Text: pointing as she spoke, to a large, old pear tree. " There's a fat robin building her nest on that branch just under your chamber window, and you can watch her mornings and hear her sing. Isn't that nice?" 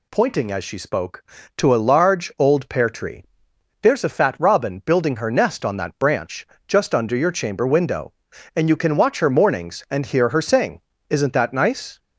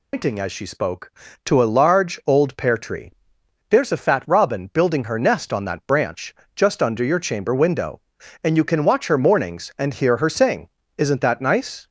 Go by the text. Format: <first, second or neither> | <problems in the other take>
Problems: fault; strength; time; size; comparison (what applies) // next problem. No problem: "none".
first | loses the start of "pointing"; at 0.1 s; 150 ms // pauses between "branch" and "just"; slight; at 6.3 s; 0.22 s long; slight in the first